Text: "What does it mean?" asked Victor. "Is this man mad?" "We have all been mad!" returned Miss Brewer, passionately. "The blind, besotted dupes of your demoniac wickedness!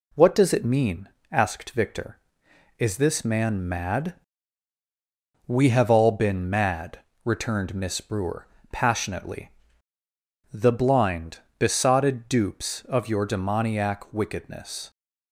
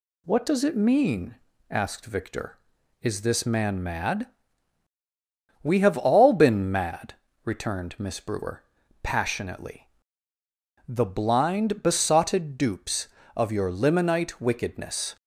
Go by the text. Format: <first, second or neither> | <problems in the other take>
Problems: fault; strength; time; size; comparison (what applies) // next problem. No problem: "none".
first | says "limonite" for "demoniac"; at 13.7 s